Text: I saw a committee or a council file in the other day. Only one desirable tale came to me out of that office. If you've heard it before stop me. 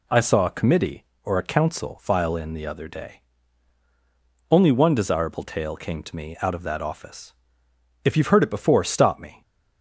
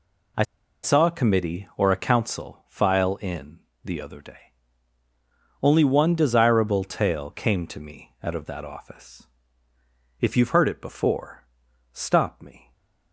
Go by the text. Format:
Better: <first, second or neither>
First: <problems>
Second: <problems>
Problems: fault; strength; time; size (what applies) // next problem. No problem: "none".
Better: first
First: none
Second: pauses between "I" and "saw"; at 0.4 s; 0.41 s long // pauses between "in" and "the"; slight; at 3.5 s; 0.26 s long // pauses between "before" and "stop"; noticeable; at 11.4 s; 0.54 s long